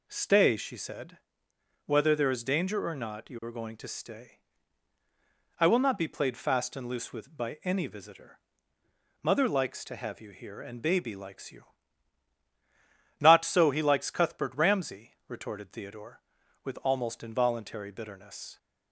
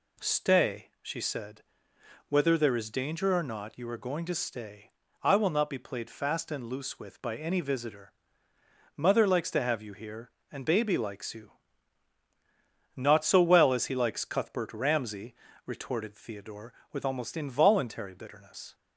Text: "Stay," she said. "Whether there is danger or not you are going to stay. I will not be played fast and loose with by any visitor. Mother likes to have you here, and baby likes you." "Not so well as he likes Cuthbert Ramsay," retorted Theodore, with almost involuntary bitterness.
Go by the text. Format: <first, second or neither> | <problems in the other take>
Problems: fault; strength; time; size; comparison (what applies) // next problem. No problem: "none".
second | skips "well as"; at 13.6 s